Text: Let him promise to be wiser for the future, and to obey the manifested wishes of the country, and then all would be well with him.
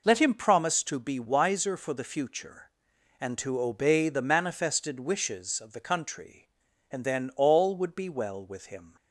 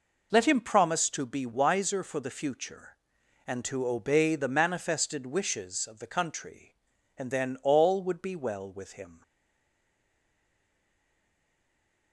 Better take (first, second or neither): first